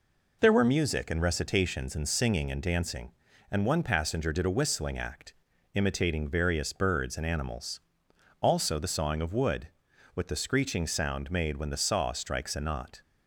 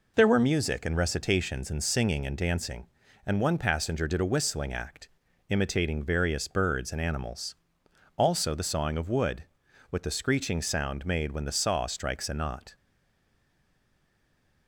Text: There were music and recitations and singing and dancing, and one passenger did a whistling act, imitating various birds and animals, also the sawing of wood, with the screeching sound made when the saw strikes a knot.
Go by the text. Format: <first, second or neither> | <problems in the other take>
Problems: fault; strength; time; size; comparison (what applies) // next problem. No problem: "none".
first | stays silent after the last word; noticeable; from 12.7 s on; 1.9 s long